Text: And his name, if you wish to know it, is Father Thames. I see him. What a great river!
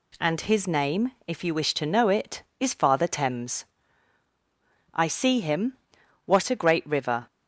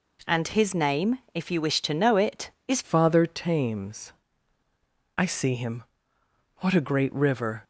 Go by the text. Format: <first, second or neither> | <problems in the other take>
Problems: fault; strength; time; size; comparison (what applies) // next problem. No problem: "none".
first | changes voice at "Father"; from 2.8 s on; 4.8 s long